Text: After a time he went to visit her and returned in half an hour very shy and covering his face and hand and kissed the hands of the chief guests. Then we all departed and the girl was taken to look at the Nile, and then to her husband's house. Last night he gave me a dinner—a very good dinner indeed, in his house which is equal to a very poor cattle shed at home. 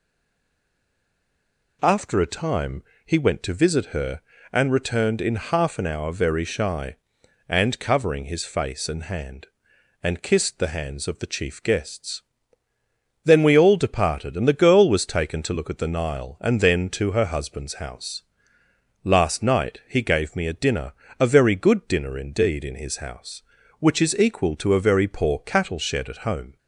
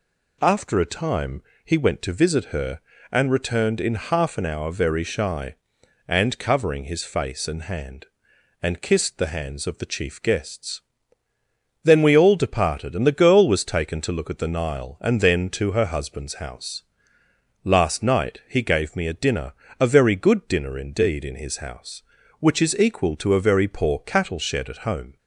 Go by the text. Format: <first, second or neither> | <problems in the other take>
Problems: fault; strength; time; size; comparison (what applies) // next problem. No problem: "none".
second | stays silent before the first word; noticeable; until 1.8 s; 1.8 s long // pauses between "time" and "he"; slight; at 2.8 s; 0.22 s long; slight in the second